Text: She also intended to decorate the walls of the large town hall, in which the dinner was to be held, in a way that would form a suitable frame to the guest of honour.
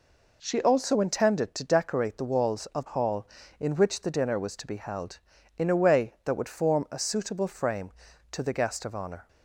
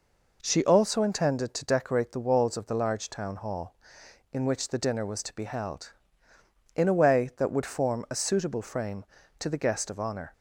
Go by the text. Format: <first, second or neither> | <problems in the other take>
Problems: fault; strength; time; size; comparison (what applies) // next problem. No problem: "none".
second | skips "the large town"; at 2.8 s